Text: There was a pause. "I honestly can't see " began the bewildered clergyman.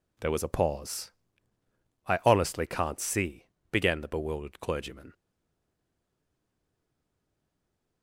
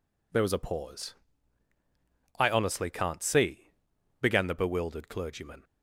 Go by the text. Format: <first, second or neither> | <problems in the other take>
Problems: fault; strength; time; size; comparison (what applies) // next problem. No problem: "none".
second | stays silent after the last word; strong; from 5.1 s on; 2.9 s long